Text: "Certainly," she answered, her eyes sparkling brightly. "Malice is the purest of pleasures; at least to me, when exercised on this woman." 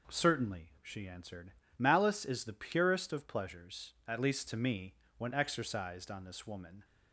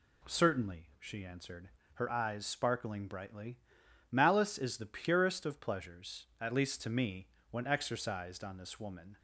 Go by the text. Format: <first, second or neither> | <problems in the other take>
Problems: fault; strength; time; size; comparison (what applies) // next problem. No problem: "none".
second | skips "her eyes sparkling brightly"; at 1.6 s